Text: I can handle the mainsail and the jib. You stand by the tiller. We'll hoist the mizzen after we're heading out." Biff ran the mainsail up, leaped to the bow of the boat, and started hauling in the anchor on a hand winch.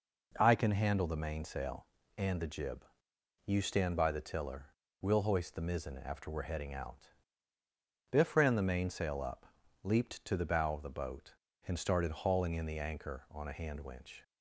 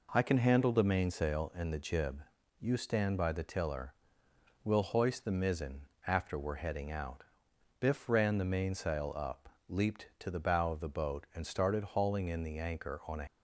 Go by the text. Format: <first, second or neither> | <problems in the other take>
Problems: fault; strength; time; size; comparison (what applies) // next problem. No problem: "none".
first | pauses between "mizzen" and "after"; slight; at 5.8 s; 0.26 s long // stops before "hand winch"; at 13.2 s